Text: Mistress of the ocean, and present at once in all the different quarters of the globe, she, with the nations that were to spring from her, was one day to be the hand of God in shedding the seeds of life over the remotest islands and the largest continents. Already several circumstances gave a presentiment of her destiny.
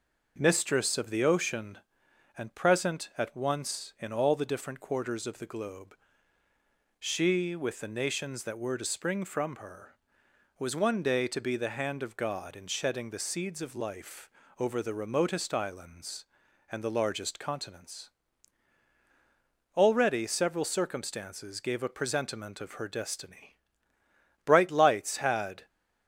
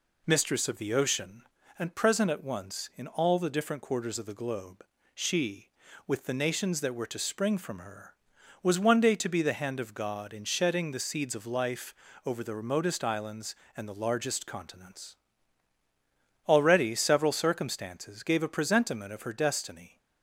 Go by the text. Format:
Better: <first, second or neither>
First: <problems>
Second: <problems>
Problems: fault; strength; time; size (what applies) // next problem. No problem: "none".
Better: second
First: pauses between "life" and "over"; slight; at 14.2 s; 0.30 s long // goes on to say "Bright lights had"; noticeable; from 24.4 s on; 1.2 s long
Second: pauses between "life" and "over"; slight; at 11.9 s; 0.32 s long